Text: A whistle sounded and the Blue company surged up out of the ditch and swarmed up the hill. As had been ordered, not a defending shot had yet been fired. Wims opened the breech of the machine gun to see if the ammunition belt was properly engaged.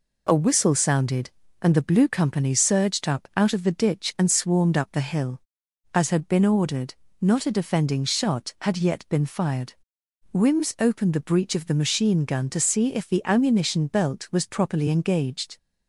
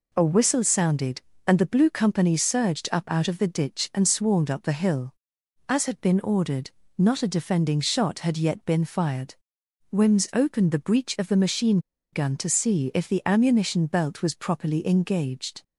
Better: first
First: none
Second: pauses between "machine" and "gun"; slight; at 11.7 s; 0.32 s long

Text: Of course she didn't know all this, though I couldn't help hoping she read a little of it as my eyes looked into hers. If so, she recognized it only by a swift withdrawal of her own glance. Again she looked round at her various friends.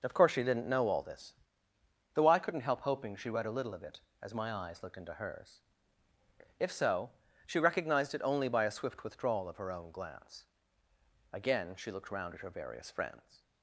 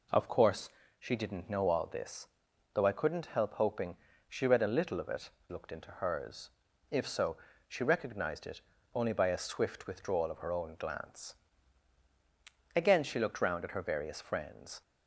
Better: first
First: none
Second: pauses between "course" and "she"; slight; at 0.7 s; 0.28 s long // pauses between "hoping" and "she"; slight; at 3.9 s; 0.32 s long // skips "as my eyes"; at 5.3 s // pauses between "it" and "only"; slight; at 8.6 s; 0.32 s long

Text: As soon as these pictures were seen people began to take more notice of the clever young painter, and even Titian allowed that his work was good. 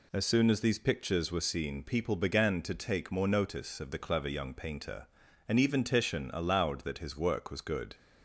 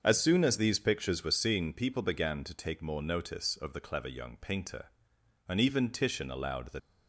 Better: first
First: none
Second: starts louder than the rest; until 1.0 s; 6.5 dB // stops before "his work was good"; at 6.7 s

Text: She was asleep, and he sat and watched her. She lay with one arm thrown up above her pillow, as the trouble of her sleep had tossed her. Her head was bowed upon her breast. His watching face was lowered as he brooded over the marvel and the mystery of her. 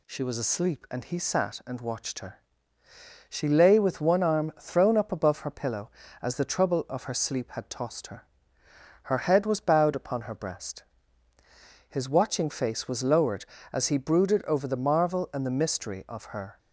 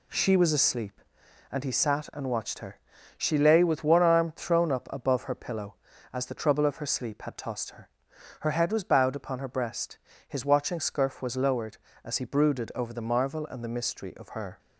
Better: first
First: none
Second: says "scurf" for "face"; at 10.7 s

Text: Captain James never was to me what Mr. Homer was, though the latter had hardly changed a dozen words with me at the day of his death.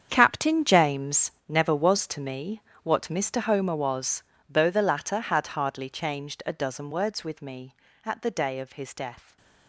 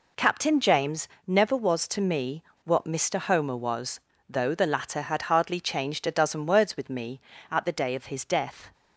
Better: second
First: gets quieter; strong; throughout; 14.5 dB // pauses between "James" and "never"; slight; at 1.2 s; 0.18 s long // pauses between "me" and "what"; slight; at 2.6 s; 0.20 s long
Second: pauses between "James" and "never"; slight; at 1.0 s; 0.18 s long // pauses between "me" and "what"; slight; at 2.4 s; 0.24 s long

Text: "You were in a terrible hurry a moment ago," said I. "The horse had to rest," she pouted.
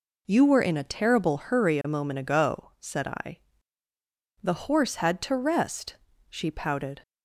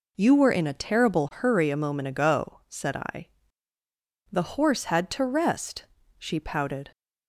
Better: neither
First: none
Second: none

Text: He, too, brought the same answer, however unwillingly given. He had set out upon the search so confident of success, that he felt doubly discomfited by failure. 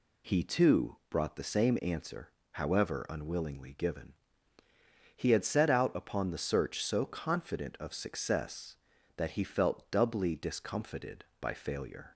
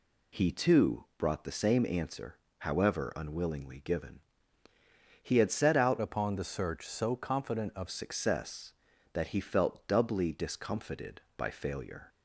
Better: first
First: none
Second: changes voice from "upon" to "of"; from 5.9 to 7.8 s; 1.9 s long

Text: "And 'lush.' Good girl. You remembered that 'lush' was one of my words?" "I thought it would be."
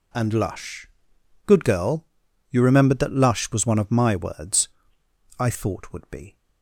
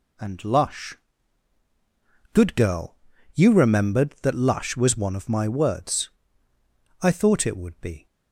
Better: second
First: skips "it"; at 5.9 s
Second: none

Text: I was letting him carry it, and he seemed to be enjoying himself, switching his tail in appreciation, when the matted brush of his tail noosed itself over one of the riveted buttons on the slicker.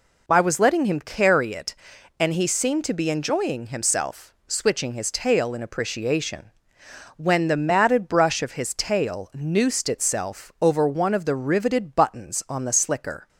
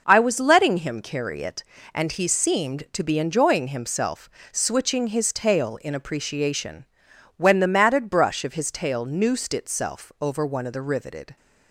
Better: first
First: none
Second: stops before "buttons on the slicker"; at 11.3 s

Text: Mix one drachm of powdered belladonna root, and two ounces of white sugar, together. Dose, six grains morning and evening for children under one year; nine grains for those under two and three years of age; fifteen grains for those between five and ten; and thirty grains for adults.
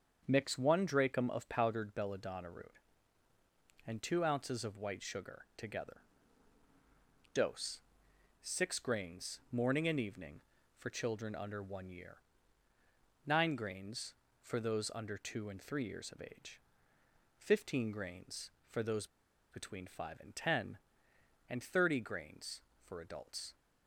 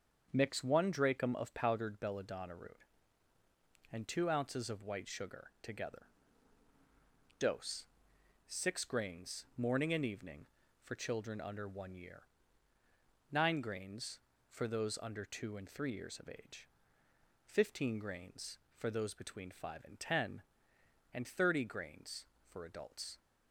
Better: second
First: starts louder than the rest; until 1.2 s; 7 dB // pauses between "those" and "between"; at 19.0 s; 0.44 s long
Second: starts louder than the rest; until 1.3 s; 7 dB

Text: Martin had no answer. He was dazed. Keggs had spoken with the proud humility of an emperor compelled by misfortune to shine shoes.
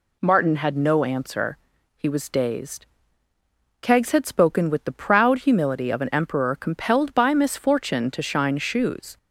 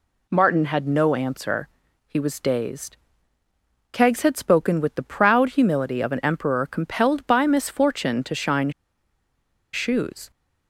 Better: first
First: none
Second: pauses between "shine" and "shoes"; at 8.6 s; 1.0 s long

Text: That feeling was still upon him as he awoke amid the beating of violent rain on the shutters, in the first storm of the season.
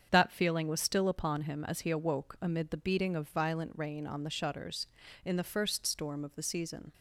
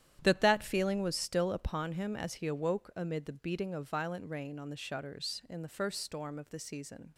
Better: first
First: starts louder than the rest; strong; until 1.1 s; 7.5 dB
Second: starts louder than the rest; strong; until 1.2 s; 11 dB // says "That" twice; at 0.4 s

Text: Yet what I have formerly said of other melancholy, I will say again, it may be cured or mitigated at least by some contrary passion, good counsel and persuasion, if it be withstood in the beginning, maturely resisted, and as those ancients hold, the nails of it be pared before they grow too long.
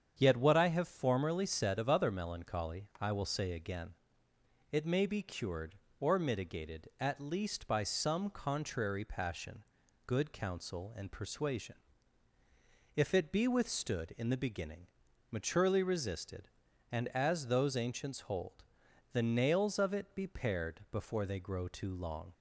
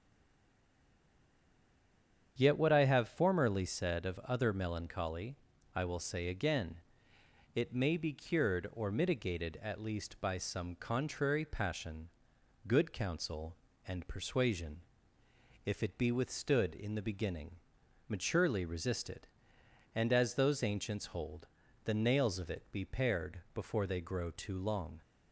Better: first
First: starts louder than the rest; strong; until 1.1 s; 8 dB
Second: stays silent before the first word; until 2.3 s; 2.3 s long // starts louder than the rest; strong; until 3.3 s; 8 dB // pauses between "pared" and "before"; slight; at 23.3 s; 0.16 s long

